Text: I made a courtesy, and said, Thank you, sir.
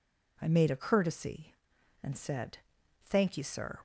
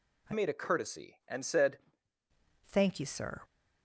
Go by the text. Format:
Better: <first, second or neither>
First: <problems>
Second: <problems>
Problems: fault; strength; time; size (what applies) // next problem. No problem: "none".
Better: first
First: none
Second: changes voice from "made" to "said"; from 0.3 to 1.7 s; 1.4 s long